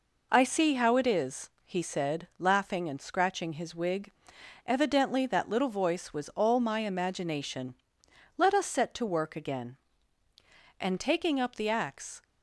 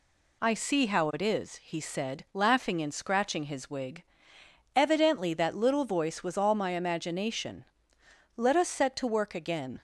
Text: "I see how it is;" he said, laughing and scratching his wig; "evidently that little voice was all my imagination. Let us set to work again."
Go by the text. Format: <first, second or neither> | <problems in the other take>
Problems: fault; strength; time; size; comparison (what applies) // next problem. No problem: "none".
second | goes on to say "And taking up the axe"; from 10.7 s on; 1.4 s long